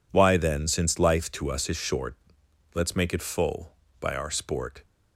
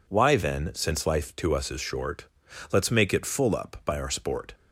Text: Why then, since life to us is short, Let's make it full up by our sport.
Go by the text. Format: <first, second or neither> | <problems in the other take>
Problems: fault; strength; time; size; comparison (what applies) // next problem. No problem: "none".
second | skips "up"; at 3.8 s